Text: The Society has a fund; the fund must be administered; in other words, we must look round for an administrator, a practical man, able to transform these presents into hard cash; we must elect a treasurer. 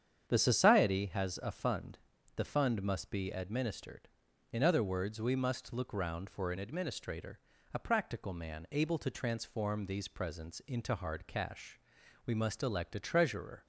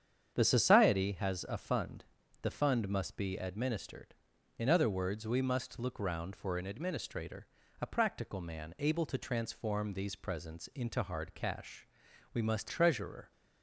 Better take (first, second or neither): first